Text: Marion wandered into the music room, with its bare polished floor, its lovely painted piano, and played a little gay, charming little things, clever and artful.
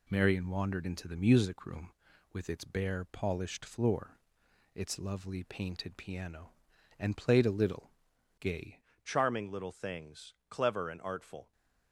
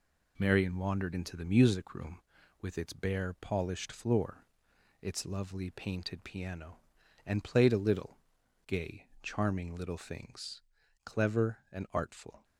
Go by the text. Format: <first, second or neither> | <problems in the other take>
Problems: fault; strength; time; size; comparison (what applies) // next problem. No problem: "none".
second | pauses between "little" and "gay"; noticeable; at 7.9 s; 0.48 s long; noticeable in the second // changes voice at "charming"; from 9.0 s on; 2.5 s long